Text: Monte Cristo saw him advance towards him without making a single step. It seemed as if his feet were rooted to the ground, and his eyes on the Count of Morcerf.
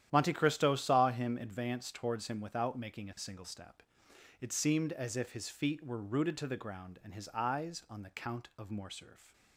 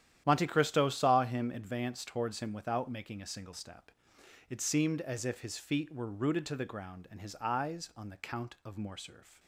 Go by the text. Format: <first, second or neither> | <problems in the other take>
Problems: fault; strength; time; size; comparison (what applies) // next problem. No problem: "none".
neither | starts louder than the rest; strong; the same in both